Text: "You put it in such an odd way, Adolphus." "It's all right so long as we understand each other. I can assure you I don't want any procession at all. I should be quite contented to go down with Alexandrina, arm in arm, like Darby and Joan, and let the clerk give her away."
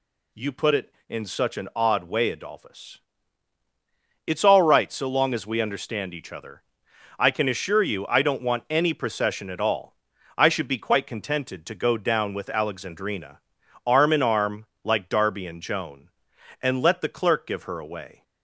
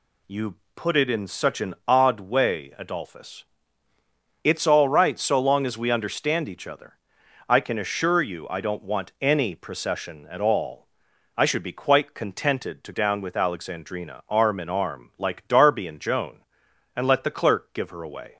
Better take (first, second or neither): first